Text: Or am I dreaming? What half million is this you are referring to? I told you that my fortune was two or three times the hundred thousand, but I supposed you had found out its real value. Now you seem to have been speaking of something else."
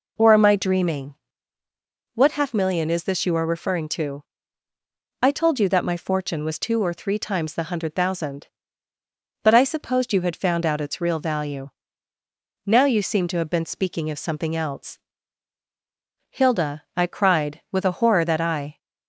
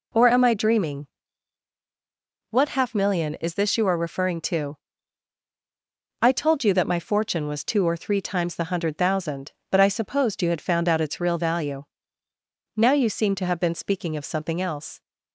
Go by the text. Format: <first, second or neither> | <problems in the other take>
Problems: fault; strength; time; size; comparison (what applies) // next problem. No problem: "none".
second | goes on to say "Hilda I cried with a horror that I"; strong; from 16.2 s on; 2.4 s long